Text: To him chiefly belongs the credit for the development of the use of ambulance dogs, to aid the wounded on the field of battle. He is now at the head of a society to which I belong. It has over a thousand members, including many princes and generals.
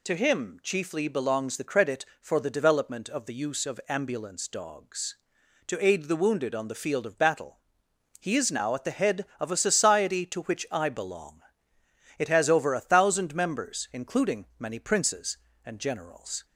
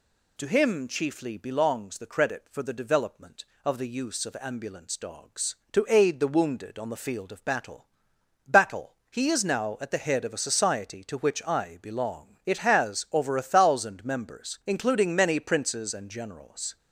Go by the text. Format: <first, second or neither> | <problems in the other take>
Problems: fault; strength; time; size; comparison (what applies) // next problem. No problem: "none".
first | says "battle" twice; at 8.4 s